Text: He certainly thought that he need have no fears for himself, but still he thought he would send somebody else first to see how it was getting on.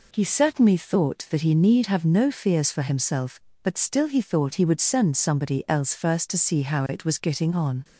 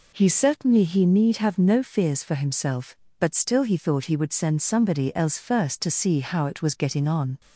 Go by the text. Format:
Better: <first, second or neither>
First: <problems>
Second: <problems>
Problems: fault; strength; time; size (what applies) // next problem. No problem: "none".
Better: first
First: none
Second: skips "thought that"; at 0.8 s